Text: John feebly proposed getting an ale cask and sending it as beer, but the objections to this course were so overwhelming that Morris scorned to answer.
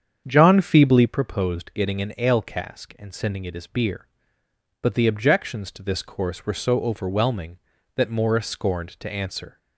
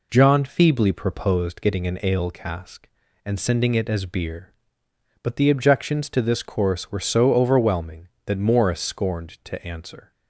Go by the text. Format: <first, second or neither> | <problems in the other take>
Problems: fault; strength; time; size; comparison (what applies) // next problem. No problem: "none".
second | starts louder than the rest; strong; until 1.1 s; 8 dB